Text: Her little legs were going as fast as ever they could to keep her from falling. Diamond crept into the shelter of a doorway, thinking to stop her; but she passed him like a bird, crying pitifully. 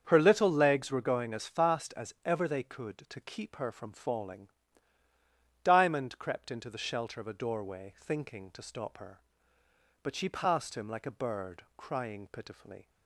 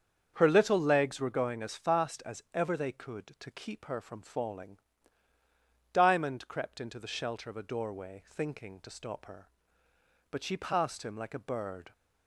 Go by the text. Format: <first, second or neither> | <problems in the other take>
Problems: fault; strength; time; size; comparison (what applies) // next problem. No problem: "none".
first | starts louder than the rest; strong; until 1.3 s; 7 dB; strong in the first // stops before "crying pitifully"; at 11.9 s